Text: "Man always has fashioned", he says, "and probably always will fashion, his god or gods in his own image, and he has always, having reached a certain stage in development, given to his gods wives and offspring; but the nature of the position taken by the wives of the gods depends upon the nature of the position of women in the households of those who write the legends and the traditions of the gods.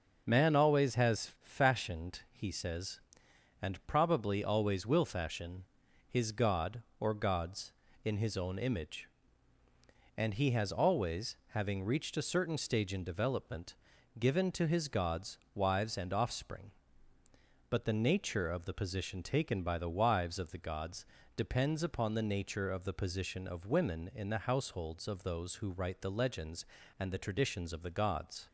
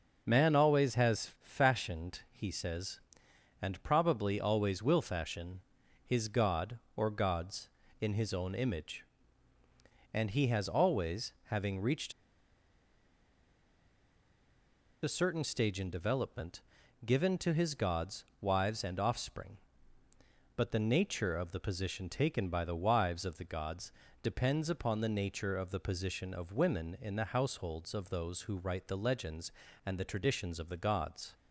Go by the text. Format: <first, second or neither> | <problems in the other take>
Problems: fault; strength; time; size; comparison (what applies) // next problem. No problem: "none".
first | pauses between "reached" and "a"; strong; at 12.1 s; 2.9 s long // pauses between "gods" and "wives"; slight; at 18.2 s; 0.16 s long; slight in the first // pauses between "gods" and "depends"; slight; at 23.9 s; 0.30 s long; slight in the first